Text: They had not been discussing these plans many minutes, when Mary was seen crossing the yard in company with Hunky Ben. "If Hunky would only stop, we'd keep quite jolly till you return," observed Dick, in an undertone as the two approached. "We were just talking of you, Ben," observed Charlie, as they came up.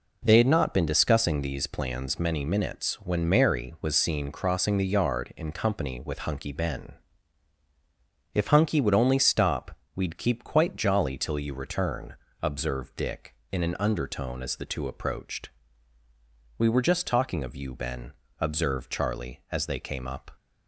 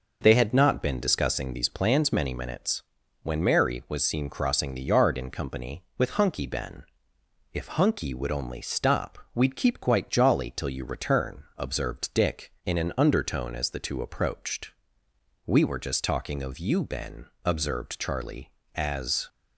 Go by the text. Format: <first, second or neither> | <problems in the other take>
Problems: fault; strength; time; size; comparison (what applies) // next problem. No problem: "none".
first | stops before "they came up"; at 19.2 s